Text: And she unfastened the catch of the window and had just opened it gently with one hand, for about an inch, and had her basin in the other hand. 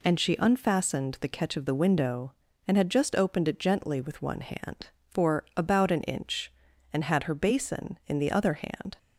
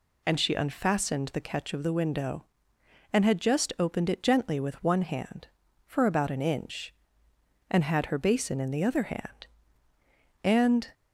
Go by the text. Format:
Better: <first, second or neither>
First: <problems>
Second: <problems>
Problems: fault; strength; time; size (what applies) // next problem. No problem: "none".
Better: first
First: none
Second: goes on to say "And"; slight; from 10.4 s on; 0.48 s long